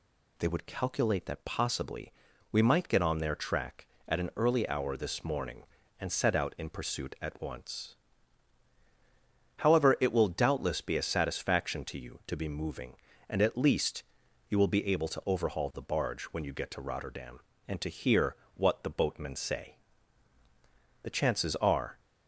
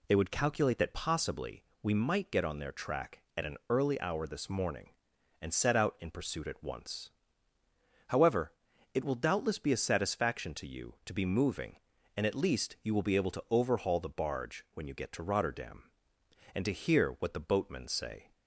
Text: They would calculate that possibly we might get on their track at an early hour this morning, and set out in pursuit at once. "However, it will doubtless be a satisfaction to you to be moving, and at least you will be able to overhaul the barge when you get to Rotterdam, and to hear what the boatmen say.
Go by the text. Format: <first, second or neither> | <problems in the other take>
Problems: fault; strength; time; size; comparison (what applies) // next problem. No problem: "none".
second | pauses between "possibly" and "we"; at 2.1 s; 0.40 s long; slight in the second // pauses between "least" and "you"; noticeable; at 14.0 s; 0.46 s long // pauses between "hear" and "what"; slight; at 18.3 s; 0.20 s long // goes on to say "The chances are"; noticeable; from 21.0 s on; 0.96 s long